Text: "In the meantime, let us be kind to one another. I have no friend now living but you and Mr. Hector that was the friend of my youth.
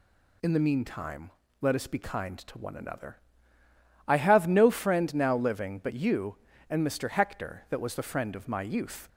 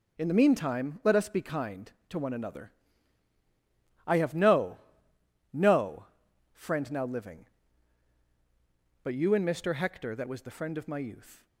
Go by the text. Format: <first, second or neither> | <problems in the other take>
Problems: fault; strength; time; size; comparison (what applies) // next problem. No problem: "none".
first | says "no" twice; at 5.5 s